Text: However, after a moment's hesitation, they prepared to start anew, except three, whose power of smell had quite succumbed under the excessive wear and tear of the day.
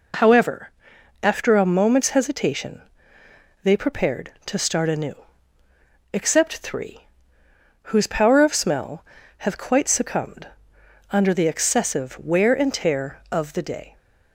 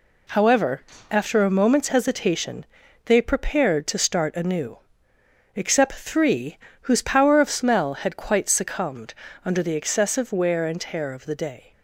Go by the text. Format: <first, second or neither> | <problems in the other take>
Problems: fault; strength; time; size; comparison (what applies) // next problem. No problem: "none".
second | says "have" for "had"; at 9.3 s // pauses between "succumbed" and "under"; noticeable; at 10.4 s; 0.64 s long; slight in the second